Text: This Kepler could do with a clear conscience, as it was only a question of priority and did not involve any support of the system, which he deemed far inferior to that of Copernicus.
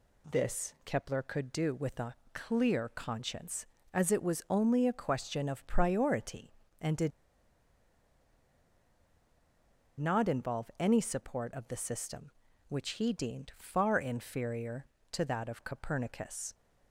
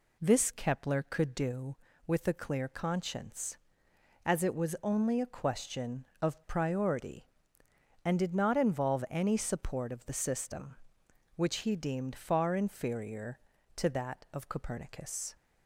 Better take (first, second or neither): second